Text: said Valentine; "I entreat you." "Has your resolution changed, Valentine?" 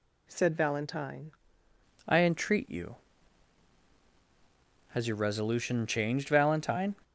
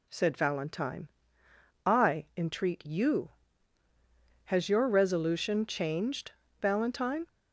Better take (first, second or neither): second